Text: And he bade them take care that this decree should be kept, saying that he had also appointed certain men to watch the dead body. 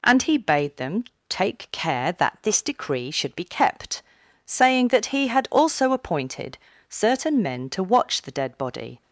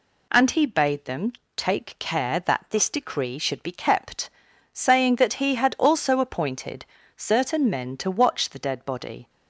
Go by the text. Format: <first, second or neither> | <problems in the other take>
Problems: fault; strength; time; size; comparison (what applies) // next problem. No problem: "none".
neither | pauses between "them" and "take"; slight; the same in both // pauses between "appointed" and "certain"; slight; the same in both